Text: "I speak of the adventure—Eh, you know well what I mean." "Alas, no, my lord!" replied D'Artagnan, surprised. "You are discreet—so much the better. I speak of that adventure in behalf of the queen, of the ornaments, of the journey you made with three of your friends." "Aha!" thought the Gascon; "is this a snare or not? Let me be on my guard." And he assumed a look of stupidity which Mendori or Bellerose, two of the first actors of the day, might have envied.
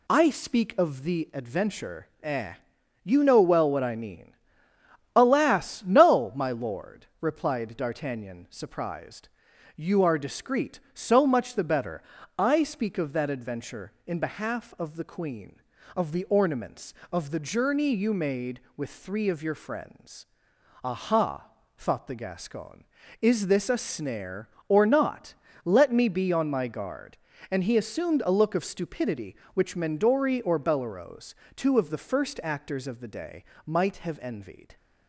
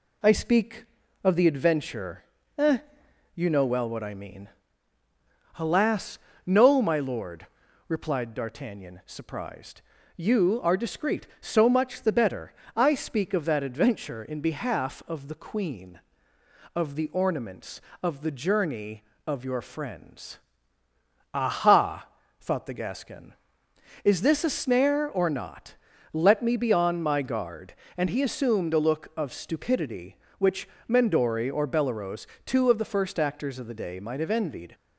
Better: first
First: none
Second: skips "you made with three"; at 19.1 s // pauses between "which" and "Mendori"; slight; at 30.6 s; 0.22 s long

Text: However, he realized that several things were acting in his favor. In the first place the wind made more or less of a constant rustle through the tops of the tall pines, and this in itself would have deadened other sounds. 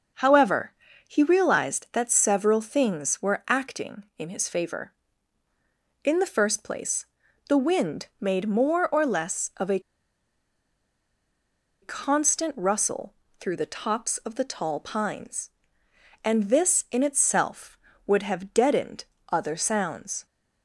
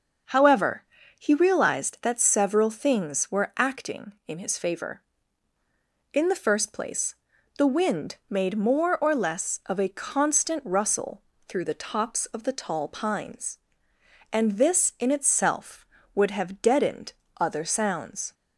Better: second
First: starts louder than the rest; noticeable; until 1.5 s; 6 dB // pauses between "place" and "the"; at 7.0 s; 0.44 s long // pauses between "a" and "constant"; strong; at 9.7 s; 2.0 s long // pauses between "rustle" and "through"; slight; at 13.1 s; 0.26 s long // pauses between "deadened" and "other"; slight; at 19.0 s; 0.26 s long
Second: starts louder than the rest; noticeable; until 1.6 s; 6 dB // pauses between "place" and "the"; at 7.1 s; 0.44 s long // pauses between "rustle" and "through"; slight; at 11.2 s; 0.26 s long // pauses between "deadened" and "other"; slight; at 17.1 s; 0.26 s long

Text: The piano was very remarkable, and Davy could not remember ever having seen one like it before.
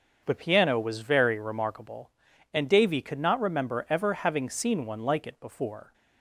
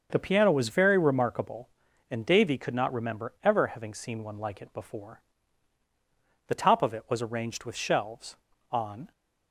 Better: first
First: starts louder than the rest; until 1.2 s; 6.5 dB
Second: starts louder than the rest; until 1.1 s; 6.5 dB // goes on to say "The top of it was arranged with shelves on"; strong; from 6.4 s on; 2.6 s long

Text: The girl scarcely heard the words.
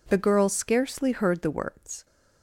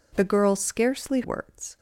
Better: first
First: none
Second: skips "heard the"; at 1.2 s

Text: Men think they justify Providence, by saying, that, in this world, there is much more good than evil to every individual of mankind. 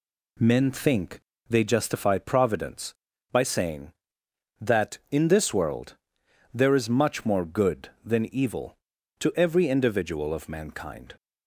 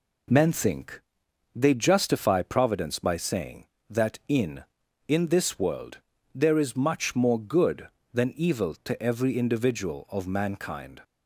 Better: first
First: pauses between "think" and "they"; slight; at 1.1 s; 0.30 s long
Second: pauses between "think" and "they"; noticeable; at 1.0 s; 0.54 s long // says "in" twice; at 5.0 s

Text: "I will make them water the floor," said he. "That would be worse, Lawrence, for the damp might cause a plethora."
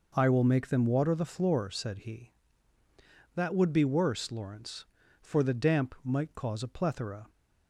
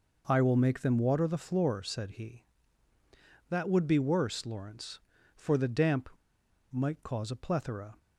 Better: first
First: none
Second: pauses between "damp" and "might"; noticeable; at 6.0 s; 0.61 s long

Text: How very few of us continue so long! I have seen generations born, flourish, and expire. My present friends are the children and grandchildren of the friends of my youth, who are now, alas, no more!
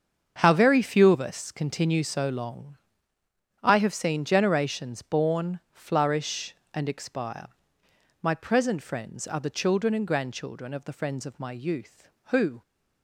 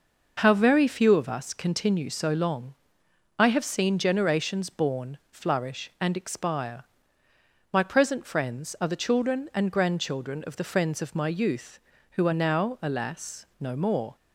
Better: second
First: starts louder than the rest; strong; until 1.4 s; 7 dB // stops before "are now alas no more"; at 12.6 s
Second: none

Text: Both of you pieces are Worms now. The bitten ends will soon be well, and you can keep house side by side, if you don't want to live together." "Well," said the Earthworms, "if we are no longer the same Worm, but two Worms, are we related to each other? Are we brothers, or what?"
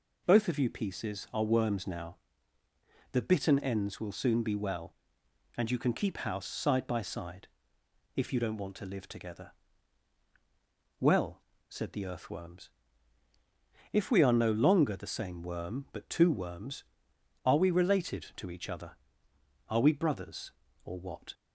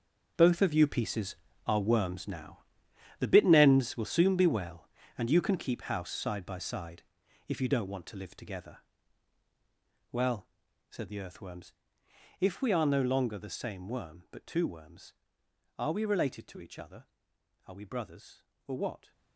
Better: first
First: none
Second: gets quieter; strong; throughout; 13 dB

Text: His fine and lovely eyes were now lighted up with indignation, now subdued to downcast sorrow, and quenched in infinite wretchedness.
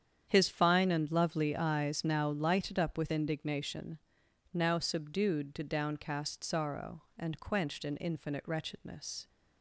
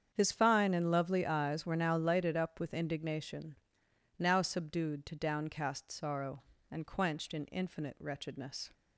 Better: second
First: starts louder than the rest; strong; until 1.3 s; 8.5 dB // skips "were"; at 2.0 s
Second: starts louder than the rest; strong; until 1.1 s; 8 dB

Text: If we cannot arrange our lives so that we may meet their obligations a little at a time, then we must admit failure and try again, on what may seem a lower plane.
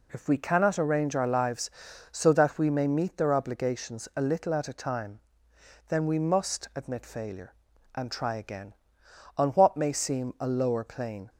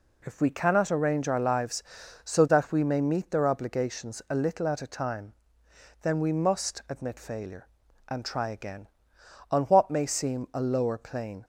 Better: neither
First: none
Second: none

